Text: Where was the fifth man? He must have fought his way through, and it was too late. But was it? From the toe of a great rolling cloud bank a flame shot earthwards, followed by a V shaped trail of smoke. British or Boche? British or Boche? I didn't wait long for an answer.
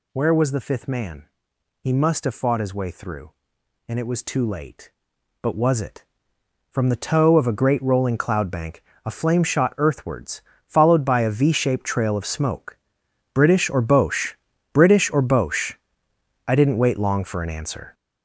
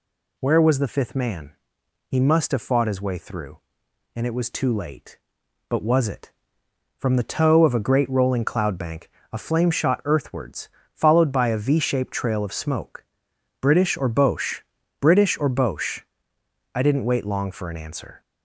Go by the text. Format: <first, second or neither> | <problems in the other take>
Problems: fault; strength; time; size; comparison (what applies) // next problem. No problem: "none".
second | gets louder; strong; throughout; 8.5 dB // pauses between "bank" and "a"; slight; at 8.8 s; 0.24 s long; slight in the second